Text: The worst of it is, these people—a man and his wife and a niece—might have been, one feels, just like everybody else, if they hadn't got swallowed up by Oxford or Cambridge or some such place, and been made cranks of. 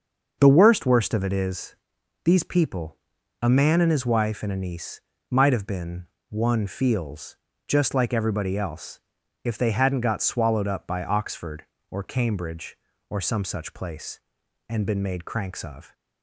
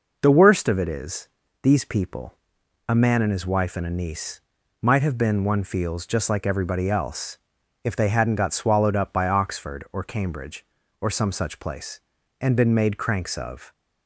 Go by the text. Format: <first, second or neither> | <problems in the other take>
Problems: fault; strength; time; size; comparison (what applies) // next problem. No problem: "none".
second | starts louder than the rest; until 1.4 s; 6 dB // says "worst" twice; at 0.8 s